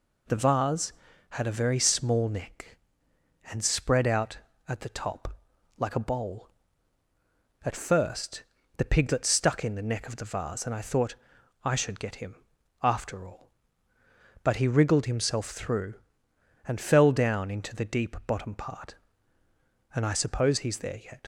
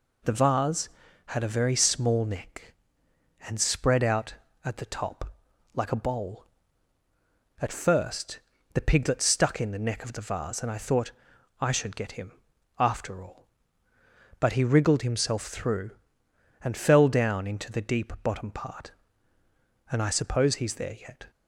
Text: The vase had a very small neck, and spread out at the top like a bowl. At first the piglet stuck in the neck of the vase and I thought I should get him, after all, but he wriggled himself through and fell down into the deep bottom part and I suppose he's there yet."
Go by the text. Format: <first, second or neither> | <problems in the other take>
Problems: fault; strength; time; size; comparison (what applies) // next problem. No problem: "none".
second | pauses between "top" and "like"; at 5.3 s; 0.42 s long; also in the second // pauses between "first" and "the"; slight; at 8.4 s; 0.34 s long; slight in the second // pauses between "thought" and "I"; noticeable; at 11.1 s; 0.50 s long; noticeable in the second // leaves "yet" unfinished; at 21.2 s; 70 ms